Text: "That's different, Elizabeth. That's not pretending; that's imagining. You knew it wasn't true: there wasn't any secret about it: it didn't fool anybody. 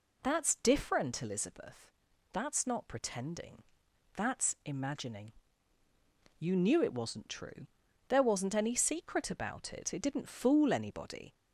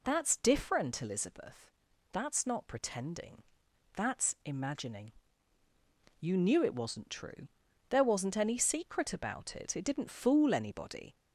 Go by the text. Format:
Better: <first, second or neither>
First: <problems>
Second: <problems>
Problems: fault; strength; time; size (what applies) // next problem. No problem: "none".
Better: neither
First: none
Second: none